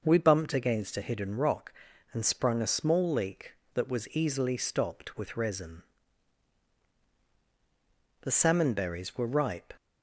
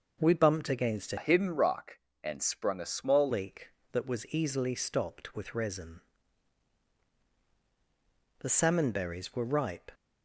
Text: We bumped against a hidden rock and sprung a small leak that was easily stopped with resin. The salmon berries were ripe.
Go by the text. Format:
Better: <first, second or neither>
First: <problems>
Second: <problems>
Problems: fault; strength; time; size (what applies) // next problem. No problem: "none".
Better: first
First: none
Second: changes voice from "hidden" to "small"; from 1.1 to 3.2 s; 2.1 s long